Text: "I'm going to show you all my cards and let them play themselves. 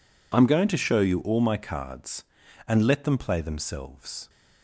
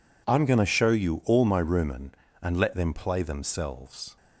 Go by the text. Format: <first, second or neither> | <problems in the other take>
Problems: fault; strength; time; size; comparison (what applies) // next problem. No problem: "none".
first | says "rumen" for "cards"; at 1.6 s